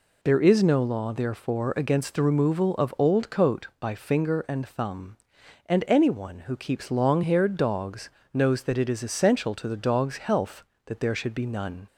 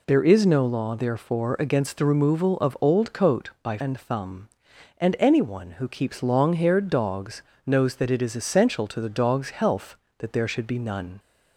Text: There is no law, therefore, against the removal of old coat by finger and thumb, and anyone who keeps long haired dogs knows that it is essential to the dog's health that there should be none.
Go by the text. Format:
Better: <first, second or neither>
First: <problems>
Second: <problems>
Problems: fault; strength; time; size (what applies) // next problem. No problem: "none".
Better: first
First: pauses between "dogs" and "knows"; slight; at 8.1 s; 0.24 s long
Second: skips "finger"; at 3.7 s // pauses between "dogs" and "knows"; slight; at 7.4 s; 0.24 s long